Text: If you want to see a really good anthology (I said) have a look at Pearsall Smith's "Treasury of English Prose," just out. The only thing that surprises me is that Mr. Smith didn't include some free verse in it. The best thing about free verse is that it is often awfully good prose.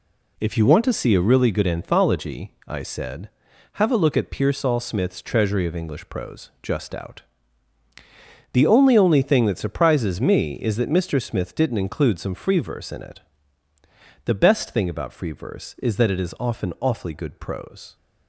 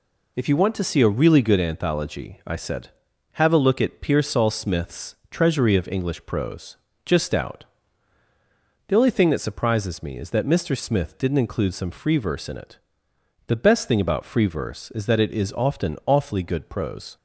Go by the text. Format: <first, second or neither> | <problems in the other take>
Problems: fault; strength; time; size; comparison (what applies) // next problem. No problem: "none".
second | says "only" twice; at 8.9 s